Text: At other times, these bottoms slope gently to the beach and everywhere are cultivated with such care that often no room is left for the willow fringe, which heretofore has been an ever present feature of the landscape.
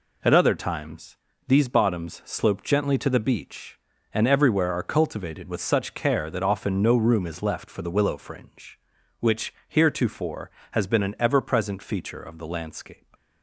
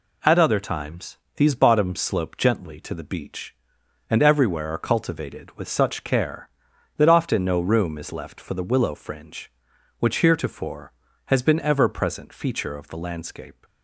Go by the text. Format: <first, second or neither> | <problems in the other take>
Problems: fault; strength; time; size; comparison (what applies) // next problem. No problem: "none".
first | skips "an"; at 11.5 s